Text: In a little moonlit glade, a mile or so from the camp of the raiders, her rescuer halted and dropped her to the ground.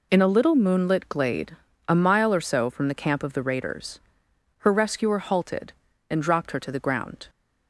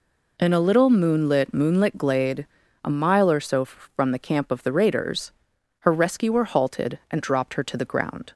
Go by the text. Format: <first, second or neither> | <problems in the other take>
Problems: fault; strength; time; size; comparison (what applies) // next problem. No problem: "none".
first | says "moonlit" twice; at 1.5 s